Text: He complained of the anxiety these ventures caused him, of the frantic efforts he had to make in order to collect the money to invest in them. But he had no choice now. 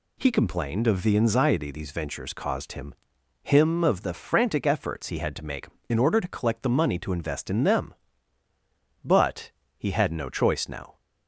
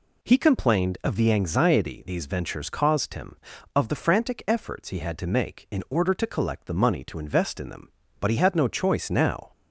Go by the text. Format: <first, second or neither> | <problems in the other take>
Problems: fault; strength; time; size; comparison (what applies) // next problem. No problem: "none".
second | says "him" twice; at 3.4 s // pauses between "But" and "he"; slight; at 9.5 s; 0.26 s long